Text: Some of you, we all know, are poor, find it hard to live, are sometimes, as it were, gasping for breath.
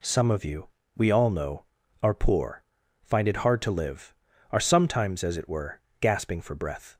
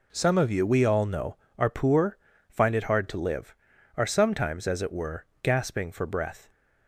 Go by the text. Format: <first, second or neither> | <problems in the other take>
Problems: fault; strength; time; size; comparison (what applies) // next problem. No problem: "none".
neither | none